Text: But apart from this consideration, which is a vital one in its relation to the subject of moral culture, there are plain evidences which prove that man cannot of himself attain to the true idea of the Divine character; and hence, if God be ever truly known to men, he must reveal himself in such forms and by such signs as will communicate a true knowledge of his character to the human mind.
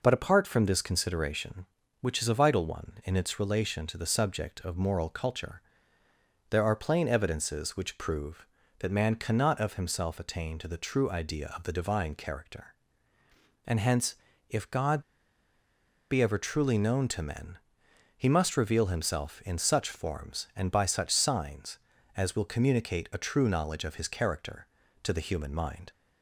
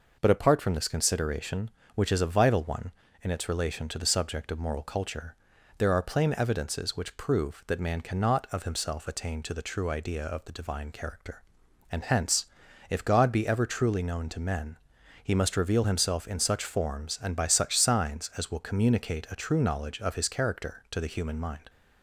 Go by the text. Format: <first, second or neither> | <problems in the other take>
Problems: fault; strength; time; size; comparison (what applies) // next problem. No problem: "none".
second | pauses between "God" and "be"; at 15.0 s; 1.1 s long